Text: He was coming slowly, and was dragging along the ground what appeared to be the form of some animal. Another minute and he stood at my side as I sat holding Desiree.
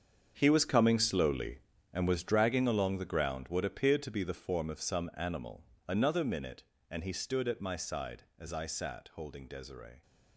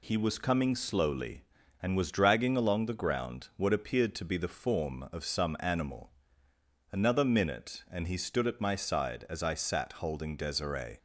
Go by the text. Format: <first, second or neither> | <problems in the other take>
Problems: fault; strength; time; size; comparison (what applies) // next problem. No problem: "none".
second | gets quieter; strong; throughout; 13.5 dB